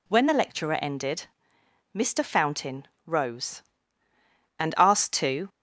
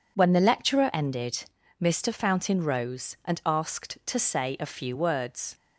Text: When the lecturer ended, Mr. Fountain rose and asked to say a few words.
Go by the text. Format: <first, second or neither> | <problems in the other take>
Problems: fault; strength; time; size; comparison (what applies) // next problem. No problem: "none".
second | pauses between "Fountain" and "rose"; slight; at 2.8 s; 0.18 s long // stops before "say a few words"; at 5.4 s